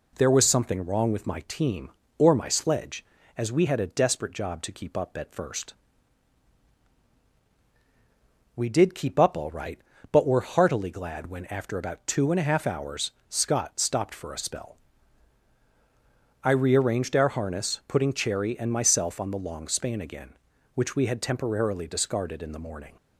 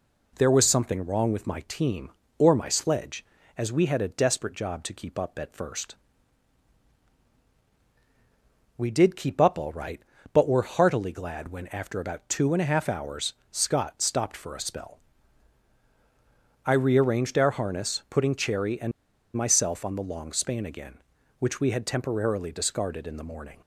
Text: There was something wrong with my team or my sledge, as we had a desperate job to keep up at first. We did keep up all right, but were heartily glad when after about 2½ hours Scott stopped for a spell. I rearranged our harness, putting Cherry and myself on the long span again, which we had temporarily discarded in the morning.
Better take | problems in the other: first | pauses between "hours" and "Scott"; slight; at 13.3 s; 0.18 s long; slight in the first // pauses between "and" and "myself"; at 18.9 s; 0.44 s long

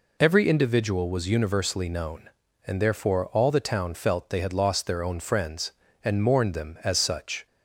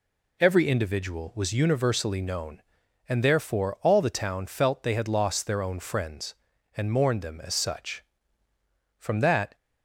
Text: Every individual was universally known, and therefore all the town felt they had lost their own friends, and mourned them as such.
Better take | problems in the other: first | goes on to say "From that"; from 8.9 s on; 0.58 s long

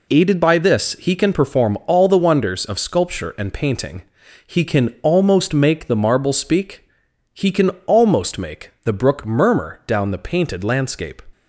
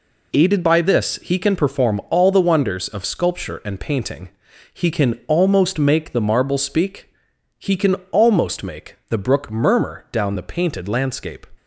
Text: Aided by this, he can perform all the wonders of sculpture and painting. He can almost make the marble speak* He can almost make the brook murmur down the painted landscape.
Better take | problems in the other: neither | pauses between "speak" and "He"; noticeable; the same in both // pauses between "can" and "almost"; slight; the same in both

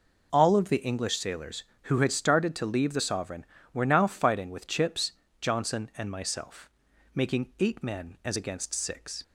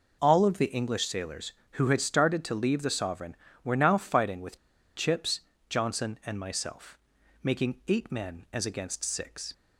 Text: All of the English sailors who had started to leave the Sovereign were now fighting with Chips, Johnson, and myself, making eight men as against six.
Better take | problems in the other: first | pauses between "with" and "Chips"; at 4.5 s; 0.39 s long

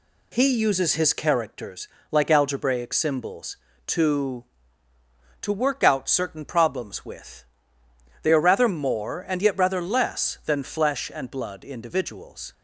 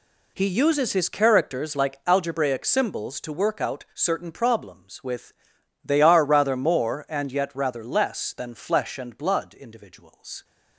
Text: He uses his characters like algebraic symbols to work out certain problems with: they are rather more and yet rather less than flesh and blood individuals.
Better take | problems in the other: second | pauses between "characters" and "like"; slight; at 1.8 s; 0.22 s long // says "to" twice; at 5.4 s

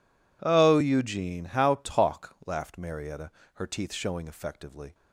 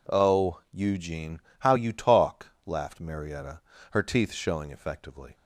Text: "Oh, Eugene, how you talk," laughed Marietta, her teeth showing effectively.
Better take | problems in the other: second | skips "you"; at 1.8 s

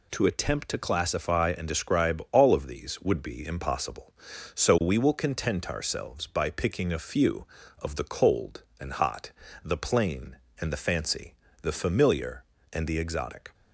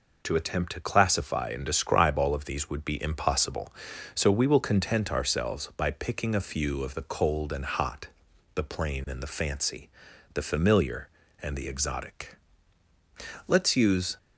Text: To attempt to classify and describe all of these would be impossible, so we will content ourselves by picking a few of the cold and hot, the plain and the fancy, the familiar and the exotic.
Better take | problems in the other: first | goes on to say "Let's use"; noticeable; from 13.4 s on; 0.70 s long

